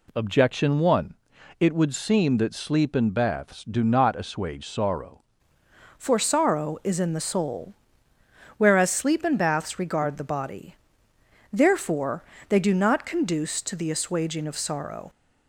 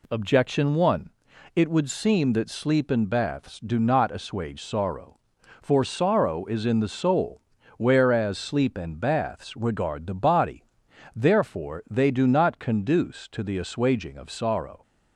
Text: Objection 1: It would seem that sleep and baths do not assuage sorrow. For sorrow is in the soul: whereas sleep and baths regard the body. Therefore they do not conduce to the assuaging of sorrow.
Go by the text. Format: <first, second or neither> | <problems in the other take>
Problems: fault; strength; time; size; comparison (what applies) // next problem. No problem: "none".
second | changes voice at "For"; from 5.9 s on; 9.1 s long // pauses between "Therefore" and "they"; slight; at 12.2 s; 0.28 s long